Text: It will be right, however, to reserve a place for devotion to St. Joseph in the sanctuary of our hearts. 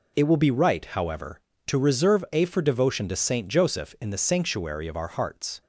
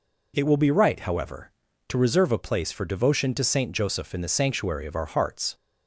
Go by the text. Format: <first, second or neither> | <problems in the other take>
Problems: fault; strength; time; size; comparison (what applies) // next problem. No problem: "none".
second | skips "place"; at 2.4 s